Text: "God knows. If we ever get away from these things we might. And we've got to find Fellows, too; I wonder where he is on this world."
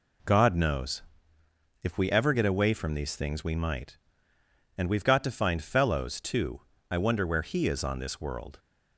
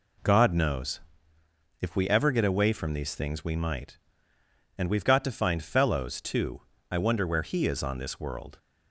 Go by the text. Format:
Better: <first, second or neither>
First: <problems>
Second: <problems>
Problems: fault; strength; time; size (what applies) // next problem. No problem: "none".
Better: neither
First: none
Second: none